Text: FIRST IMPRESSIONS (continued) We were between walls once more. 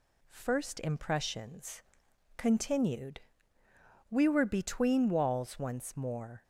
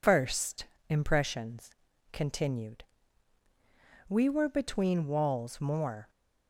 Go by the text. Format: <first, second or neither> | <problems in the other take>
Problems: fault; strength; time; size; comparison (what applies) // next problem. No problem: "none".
first | pauses between "FIRST" and "IMPRESSIONS"; slight; at 0.6 s; 0.24 s long // skips "once"; at 5.6 s